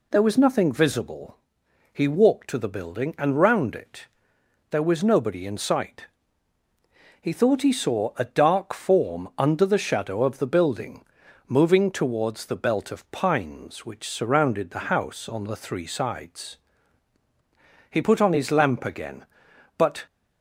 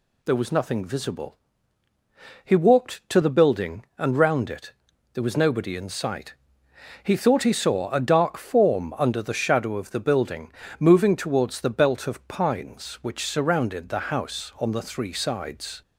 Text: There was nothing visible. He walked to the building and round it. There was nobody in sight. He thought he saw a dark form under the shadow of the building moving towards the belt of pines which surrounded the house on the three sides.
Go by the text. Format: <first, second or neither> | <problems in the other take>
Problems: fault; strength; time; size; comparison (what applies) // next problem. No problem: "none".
second | pauses between "building" and "moving"; noticeable; at 11.0 s; 0.46 s long; slight in the second // goes on to say "He put on his lamp again but"; strong; from 17.8 s on; 2.1 s long